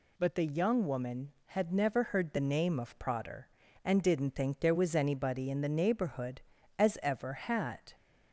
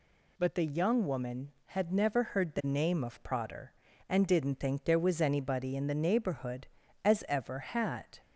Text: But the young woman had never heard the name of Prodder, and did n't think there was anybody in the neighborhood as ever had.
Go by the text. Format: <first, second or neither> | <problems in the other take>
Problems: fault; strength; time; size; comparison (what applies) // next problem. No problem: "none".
neither | none